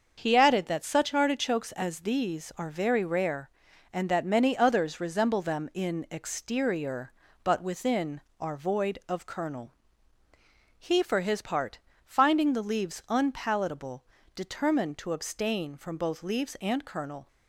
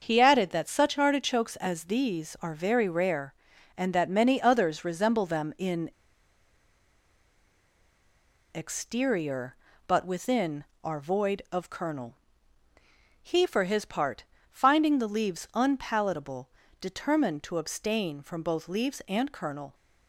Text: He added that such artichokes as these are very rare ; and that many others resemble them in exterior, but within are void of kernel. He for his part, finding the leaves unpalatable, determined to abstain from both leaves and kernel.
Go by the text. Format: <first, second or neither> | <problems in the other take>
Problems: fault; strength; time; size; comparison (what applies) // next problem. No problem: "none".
first | starts louder than the rest; until 1.0 s; 6.5 dB; also in the first // pauses between "in" and "exterior"; strong; at 5.9 s; 2.6 s long